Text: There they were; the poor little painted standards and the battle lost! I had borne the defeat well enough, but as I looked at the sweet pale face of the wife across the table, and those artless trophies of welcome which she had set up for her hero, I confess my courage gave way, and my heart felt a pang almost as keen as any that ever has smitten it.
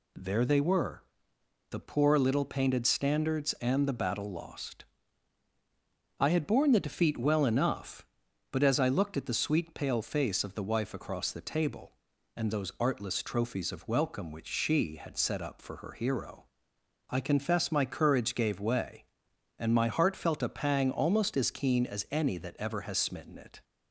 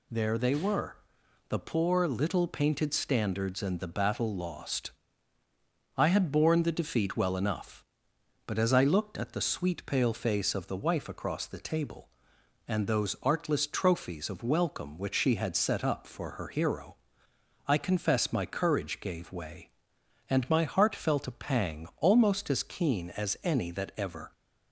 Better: first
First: none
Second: stops before "has smitten it"; at 24.3 s

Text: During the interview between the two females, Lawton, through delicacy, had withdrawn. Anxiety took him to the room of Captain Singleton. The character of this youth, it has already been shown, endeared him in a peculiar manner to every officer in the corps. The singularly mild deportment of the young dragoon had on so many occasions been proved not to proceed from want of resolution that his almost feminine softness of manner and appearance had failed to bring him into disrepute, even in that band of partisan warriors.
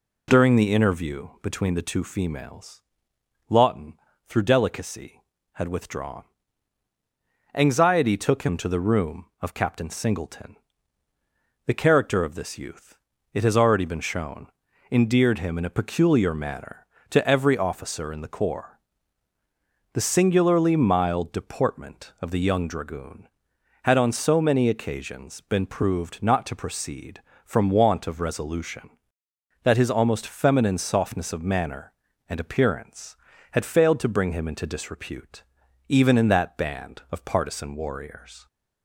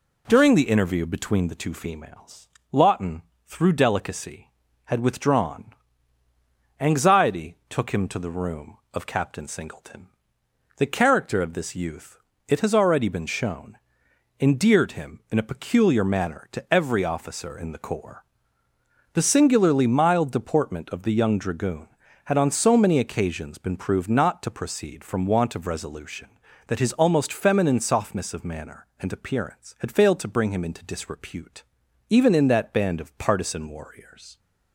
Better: neither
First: none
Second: none

